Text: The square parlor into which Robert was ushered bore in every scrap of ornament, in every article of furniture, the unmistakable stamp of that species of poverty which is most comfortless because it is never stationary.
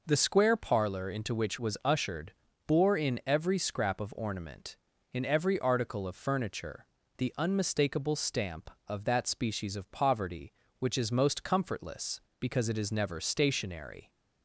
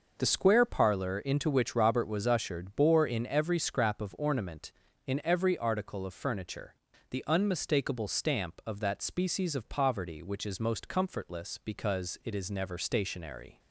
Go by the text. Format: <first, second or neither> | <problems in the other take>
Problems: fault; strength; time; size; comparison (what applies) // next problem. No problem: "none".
second | skips "Robert"; at 1.5 s // pauses between "ushered" and "bore"; slight; at 2.3 s; 0.34 s long